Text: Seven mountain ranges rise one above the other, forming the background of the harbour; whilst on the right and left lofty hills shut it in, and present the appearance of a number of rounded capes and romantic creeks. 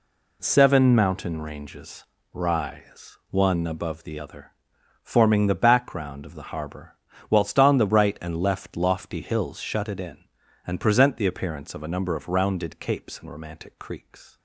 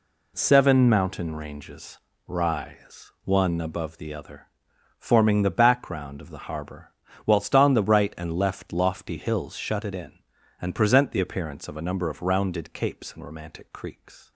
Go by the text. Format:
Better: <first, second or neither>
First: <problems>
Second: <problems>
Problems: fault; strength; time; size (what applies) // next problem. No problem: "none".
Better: neither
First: pauses between "ranges" and "rise"; slight; at 2.0 s; 0.26 s long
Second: pauses between "ranges" and "rise"; slight; at 1.9 s; 0.26 s long